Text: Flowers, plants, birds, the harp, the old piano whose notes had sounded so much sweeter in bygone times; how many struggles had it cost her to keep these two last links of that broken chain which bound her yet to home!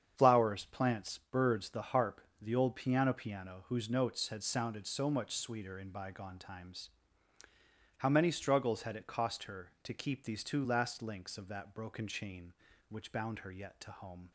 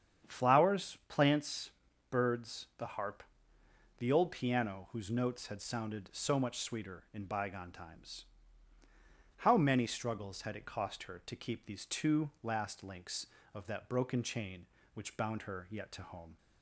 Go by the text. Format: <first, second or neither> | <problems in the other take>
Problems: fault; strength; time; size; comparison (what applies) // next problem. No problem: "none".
second | starts louder than the rest; strong; until 1.1 s; 8 dB; strong in the second // says "piano" twice; at 3.1 s